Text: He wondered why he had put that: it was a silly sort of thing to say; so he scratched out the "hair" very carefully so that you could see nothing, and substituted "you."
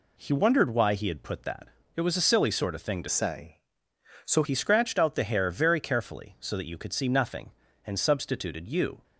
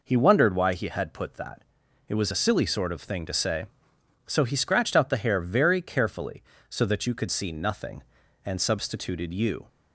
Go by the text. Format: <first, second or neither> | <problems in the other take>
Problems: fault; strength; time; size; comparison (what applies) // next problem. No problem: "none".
second | changes voice from "say" to "so"; from 3.0 to 4.4 s; 1.4 s long